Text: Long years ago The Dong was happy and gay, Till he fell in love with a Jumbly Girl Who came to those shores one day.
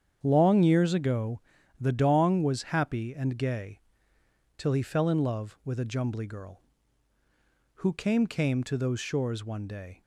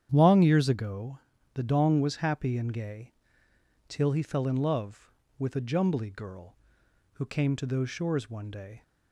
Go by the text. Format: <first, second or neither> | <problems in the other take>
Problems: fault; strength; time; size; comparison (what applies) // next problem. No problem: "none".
second | starts louder than the rest; strong; until 1.2 s; 8 dB; strong in the second // pauses between "ago" and "The"; at 1.3 s; 0.40 s long; slight in the second // says "came" twice; at 8.2 s